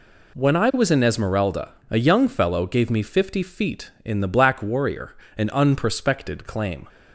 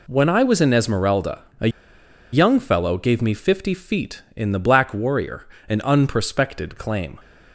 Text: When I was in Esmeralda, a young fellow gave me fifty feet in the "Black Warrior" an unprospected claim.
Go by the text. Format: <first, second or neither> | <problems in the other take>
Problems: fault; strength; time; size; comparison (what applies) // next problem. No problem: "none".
first | pauses between "a" and "young"; noticeable; at 1.6 s; 0.64 s long // pauses between "Warrior" and "an"; slight; at 5.4 s; 0.22 s long; slight in the first